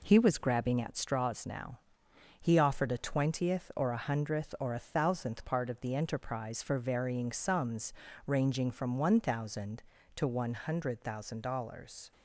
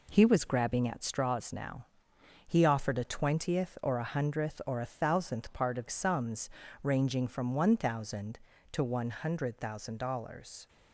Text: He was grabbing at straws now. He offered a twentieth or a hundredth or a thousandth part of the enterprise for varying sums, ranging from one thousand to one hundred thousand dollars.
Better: first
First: none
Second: skips "the enterprise for varying"; at 5.8 s

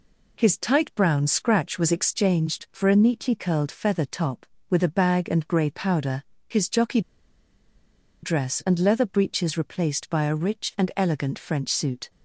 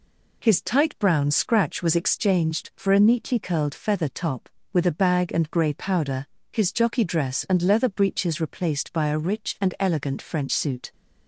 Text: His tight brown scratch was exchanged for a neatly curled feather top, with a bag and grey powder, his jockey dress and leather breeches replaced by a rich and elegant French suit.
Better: second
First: pauses between "jockey" and "dress"; at 6.9 s; 1.2 s long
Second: none

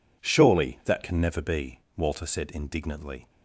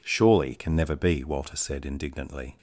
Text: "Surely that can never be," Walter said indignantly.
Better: first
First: none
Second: skips "that"; at 0.5 s

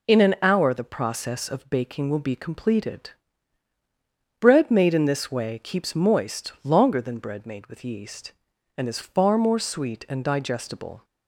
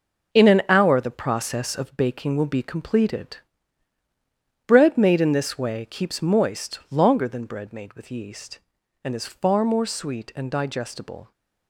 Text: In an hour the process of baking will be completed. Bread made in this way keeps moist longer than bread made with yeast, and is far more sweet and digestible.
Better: first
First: none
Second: gets quieter; strong; throughout; 9.5 dB

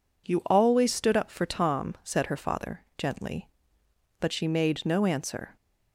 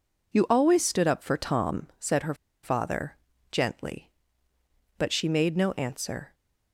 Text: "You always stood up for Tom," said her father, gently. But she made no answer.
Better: first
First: none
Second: pauses between "her" and "father"; slight; at 2.3 s; 0.29 s long

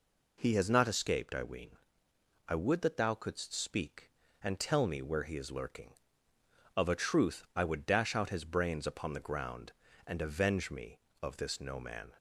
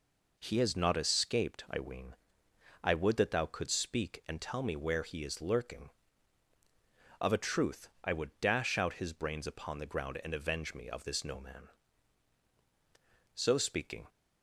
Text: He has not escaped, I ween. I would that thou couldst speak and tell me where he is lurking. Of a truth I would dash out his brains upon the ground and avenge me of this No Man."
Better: first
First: none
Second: pauses between "truth" and "I"; slight; at 7.8 s; 0.16 s long // goes on to say "So speaking"; noticeable; from 13.3 s on; 0.74 s long

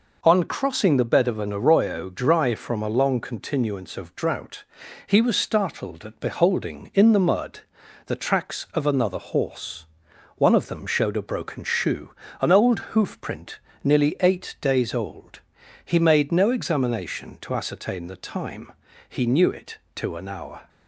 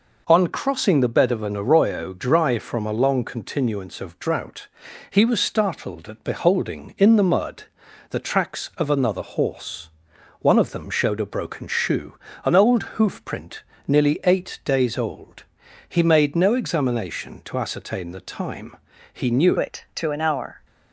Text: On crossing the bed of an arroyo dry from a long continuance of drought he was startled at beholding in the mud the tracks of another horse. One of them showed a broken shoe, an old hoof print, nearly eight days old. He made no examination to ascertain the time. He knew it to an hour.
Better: first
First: pauses between "drought" and "he"; at 4.6 s; 0.42 s long // pauses between "mud" and "the"; at 7.6 s; 0.44 s long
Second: pauses between "drought" and "he"; at 4.6 s; 0.42 s long // pauses between "mud" and "the"; at 7.6 s; 0.44 s long // changes voice at "it"; from 19.5 s on; 1.1 s long

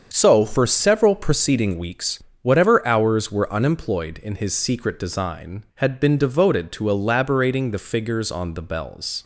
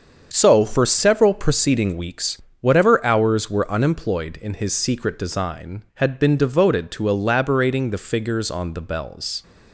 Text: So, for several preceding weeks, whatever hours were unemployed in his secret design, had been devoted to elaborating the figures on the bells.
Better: neither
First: starts louder than the rest; until 1.1 s; 7 dB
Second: starts louder than the rest; until 1.3 s; 7 dB

